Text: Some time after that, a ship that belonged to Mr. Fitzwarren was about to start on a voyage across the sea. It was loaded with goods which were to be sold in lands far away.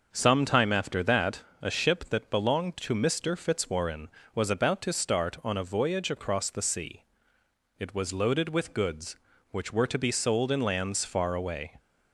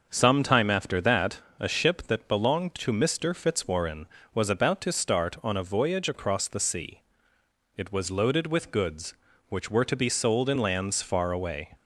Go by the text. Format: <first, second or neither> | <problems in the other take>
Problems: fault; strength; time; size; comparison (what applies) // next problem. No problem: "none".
neither | starts louder than the rest; noticeable; the same in both